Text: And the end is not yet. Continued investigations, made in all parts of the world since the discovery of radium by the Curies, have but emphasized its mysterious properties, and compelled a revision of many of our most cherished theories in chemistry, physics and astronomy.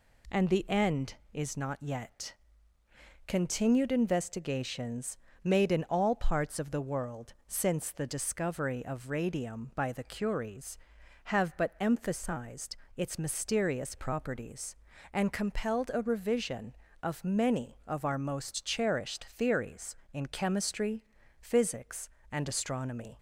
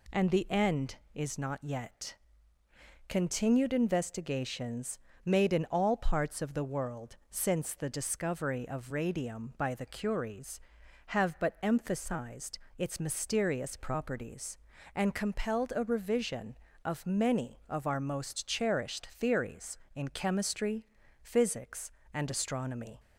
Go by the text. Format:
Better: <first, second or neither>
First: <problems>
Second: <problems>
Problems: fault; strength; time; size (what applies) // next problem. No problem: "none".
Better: neither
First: pauses between "emphasized" and "its"; slight; at 12.7 s; 0.20 s long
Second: pauses between "emphasized" and "its"; slight; at 12.5 s; 0.19 s long